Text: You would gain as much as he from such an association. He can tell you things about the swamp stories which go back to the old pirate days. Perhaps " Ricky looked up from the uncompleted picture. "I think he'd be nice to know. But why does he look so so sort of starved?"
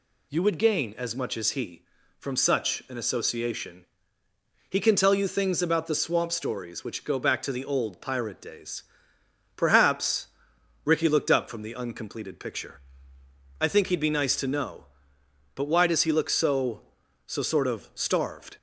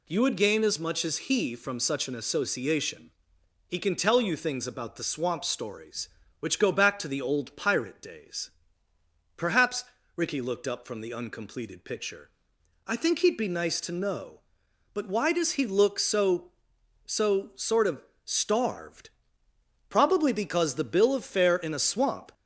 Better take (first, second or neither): first